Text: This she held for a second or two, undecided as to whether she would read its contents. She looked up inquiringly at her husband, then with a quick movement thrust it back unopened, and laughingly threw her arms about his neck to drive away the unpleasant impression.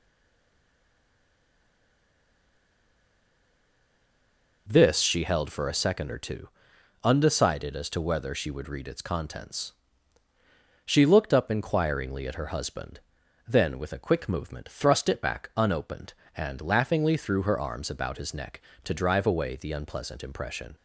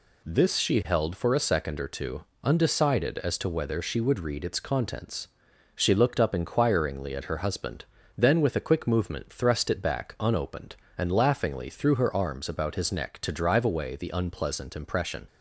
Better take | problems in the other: second | stays silent before the first word; strong; until 4.6 s; 4.6 s long

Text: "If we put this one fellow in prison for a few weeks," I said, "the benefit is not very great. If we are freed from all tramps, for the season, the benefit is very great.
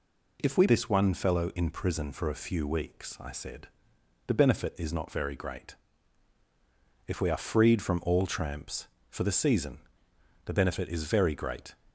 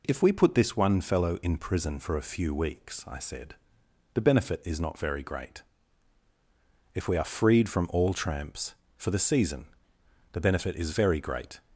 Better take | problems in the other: second | skips "put"; at 0.6 s

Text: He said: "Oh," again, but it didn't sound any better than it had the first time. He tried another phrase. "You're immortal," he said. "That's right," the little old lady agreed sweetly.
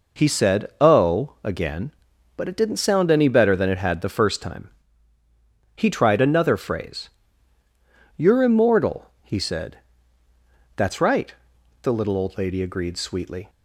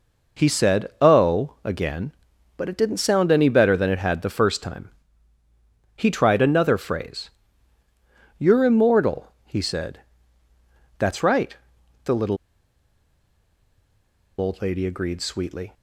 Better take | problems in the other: first | pauses between "little" and "old"; strong; at 12.3 s; 2.0 s long

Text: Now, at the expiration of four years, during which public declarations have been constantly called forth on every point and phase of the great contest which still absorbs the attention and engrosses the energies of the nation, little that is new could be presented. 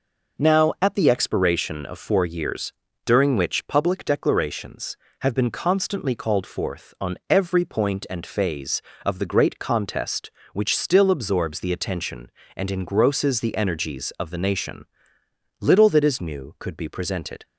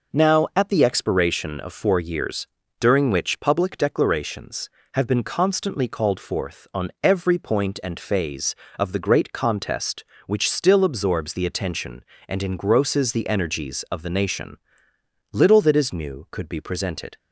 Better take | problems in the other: neither | none

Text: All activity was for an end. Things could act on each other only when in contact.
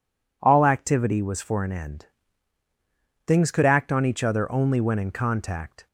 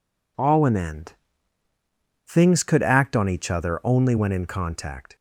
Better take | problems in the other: first | skips "activity was for"; at 0.6 s

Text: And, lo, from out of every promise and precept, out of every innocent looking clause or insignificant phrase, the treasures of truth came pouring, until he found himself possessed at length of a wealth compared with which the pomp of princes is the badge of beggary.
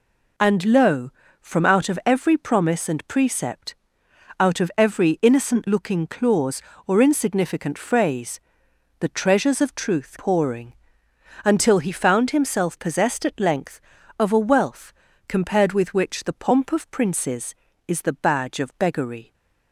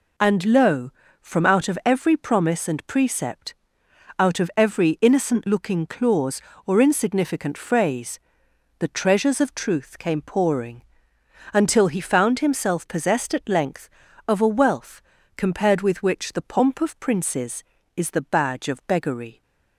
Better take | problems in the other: second | skips "came"; at 10.1 s // pauses between "wealth" and "compared"; slight; at 14.9 s; 0.34 s long; slight in the second

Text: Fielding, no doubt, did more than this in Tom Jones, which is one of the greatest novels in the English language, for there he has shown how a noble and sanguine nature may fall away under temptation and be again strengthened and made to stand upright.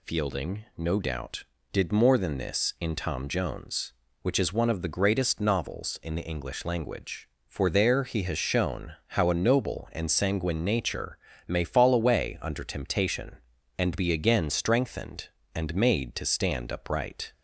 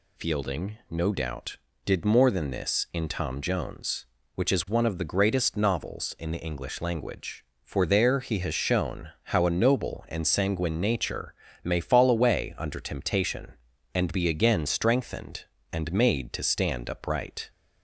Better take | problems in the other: neither | pauses between "nature" and "may"; slight; the same in both

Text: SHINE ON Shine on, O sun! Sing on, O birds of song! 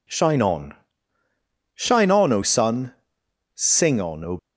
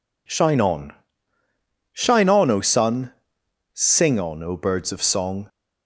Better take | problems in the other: second | pauses between "ON" and "Shine"; at 0.7 s; 1.0 s long; also in the second // stops before "birds of song"; at 4.3 s

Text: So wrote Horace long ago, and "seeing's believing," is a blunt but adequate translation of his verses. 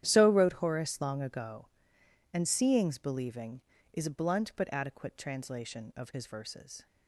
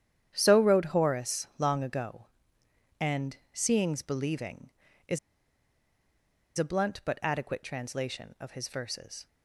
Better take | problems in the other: first | starts louder than the rest; strong; until 1.3 s; 10 dB; strong in the first // pauses between "and" and "seeing's"; slight; at 3.3 s; 0.16 s long // pauses between "is" and "a"; strong; at 5.1 s; 1.3 s long

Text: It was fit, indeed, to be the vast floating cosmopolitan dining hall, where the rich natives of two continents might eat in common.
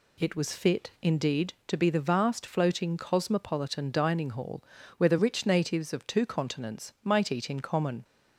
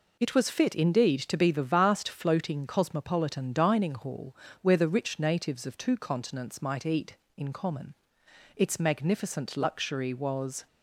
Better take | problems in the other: first | goes on to say "Its magnificent luxury was"; strong; from 8.5 s on; 2.1 s long

